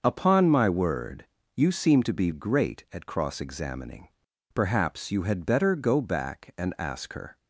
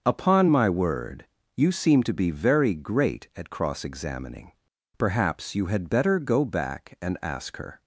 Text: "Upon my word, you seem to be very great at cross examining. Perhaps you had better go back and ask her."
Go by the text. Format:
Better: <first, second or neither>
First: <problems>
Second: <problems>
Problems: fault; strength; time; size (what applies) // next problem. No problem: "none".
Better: second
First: starts louder than the rest; until 1.0 s; 6 dB // skips "very"; at 2.3 s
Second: starts louder than the rest; until 1.0 s; 6.5 dB